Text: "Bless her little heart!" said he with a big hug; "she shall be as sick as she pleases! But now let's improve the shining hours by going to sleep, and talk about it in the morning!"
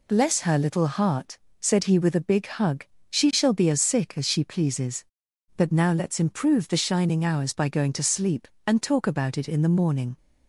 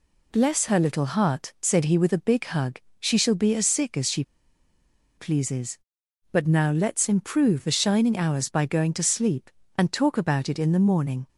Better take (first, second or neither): first